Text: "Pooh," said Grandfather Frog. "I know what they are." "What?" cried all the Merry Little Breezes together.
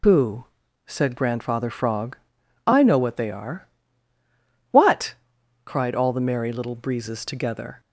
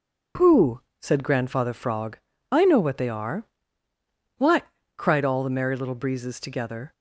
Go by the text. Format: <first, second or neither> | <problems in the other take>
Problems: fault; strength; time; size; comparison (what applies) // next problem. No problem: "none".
second | loses the start of "Pooh"; at 0.0 s; 95 ms